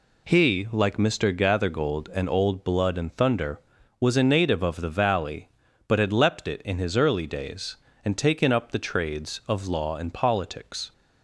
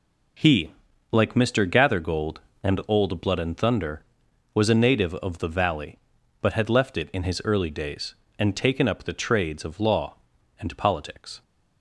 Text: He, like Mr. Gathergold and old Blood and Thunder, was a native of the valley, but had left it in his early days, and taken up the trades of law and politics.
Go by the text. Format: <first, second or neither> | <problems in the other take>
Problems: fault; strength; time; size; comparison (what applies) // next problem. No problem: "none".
second | says "leapt" for "left"; at 6.1 s